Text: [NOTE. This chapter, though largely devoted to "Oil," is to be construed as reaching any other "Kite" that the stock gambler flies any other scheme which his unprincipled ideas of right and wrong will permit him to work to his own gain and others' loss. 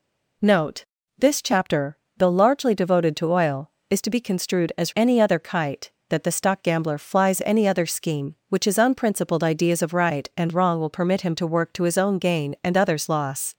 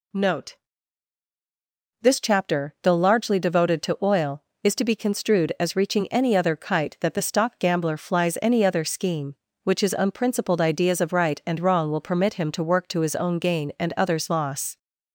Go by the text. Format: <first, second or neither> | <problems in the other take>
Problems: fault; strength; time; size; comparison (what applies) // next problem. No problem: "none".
second | skips "reaching"; at 4.9 s